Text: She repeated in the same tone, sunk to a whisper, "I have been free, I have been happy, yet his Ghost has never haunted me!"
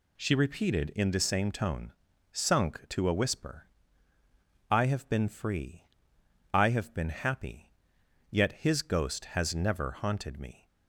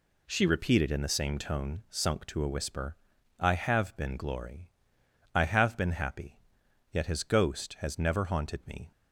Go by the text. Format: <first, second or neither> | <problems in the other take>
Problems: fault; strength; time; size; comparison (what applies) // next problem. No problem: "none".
first | says "glory" for "free"; at 4.1 s